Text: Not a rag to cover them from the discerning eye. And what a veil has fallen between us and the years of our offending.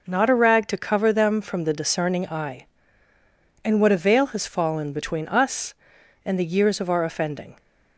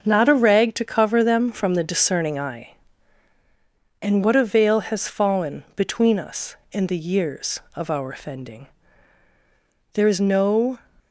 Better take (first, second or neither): first